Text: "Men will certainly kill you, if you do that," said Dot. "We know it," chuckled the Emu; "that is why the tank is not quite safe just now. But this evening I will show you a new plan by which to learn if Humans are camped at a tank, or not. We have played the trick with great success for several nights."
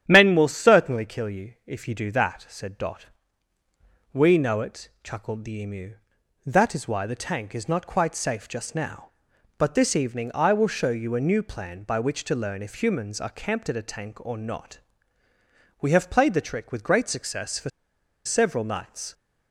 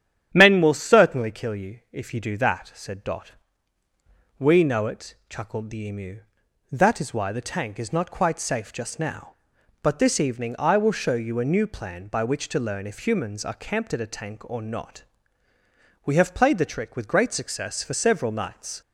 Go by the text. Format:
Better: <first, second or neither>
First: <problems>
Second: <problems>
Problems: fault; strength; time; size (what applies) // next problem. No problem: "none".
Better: second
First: starts louder than the rest; strong; until 1.0 s; 10 dB // pauses between "for" and "several"; noticeable; at 17.6 s; 0.55 s long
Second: starts louder than the rest; strong; until 1.3 s; 10 dB